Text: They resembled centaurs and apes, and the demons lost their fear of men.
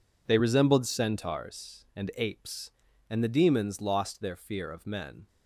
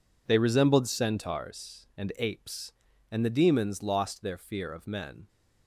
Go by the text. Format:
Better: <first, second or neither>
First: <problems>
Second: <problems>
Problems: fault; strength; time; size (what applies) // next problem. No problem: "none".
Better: neither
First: none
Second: none